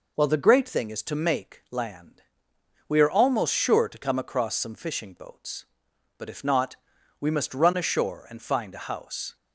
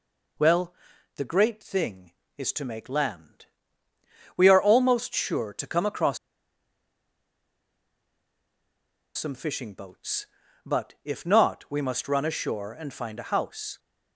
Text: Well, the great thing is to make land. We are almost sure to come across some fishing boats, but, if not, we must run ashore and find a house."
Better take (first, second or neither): first